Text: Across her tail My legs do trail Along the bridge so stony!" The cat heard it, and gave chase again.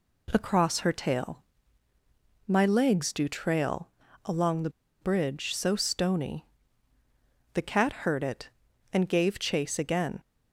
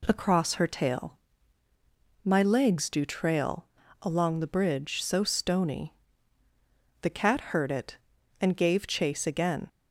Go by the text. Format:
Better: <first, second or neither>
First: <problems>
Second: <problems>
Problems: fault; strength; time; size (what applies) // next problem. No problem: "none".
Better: second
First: pauses between "tail" and "My"; at 1.4 s; 1.0 s long // pauses between "trail" and "Along"; slight; at 3.8 s; 0.36 s long // pauses between "the" and "bridge"; slight; at 4.6 s; 0.32 s long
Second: pauses between "tail" and "My"; at 1.1 s; 1.0 s long // pauses between "trail" and "Along"; slight; at 3.6 s; 0.36 s long